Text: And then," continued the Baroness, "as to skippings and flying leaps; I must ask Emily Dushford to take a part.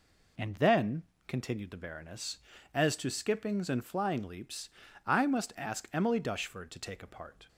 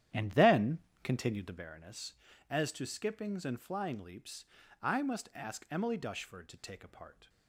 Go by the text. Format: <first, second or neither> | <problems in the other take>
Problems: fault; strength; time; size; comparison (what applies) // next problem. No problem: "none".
first | starts louder than the rest; strong; until 1.7 s; 10.5 dB